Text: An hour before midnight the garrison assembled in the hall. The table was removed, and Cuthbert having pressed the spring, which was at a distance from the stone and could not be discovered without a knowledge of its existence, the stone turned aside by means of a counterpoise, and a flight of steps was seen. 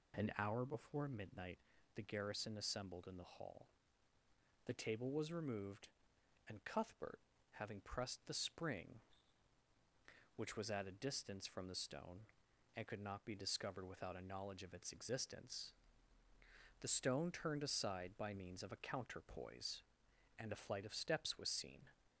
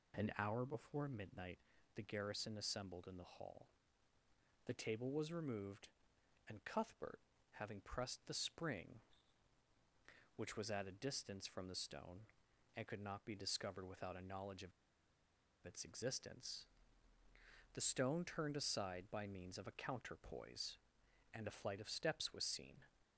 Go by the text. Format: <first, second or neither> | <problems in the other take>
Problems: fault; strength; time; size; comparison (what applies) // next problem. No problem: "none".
first | pauses between "midnight" and "the"; at 1.5 s; 0.40 s long; also in the first // pauses between "Cuthbert" and "having"; at 7.1 s; 0.40 s long; also in the first // pauses between "of" and "its"; noticeable; at 14.7 s; 0.93 s long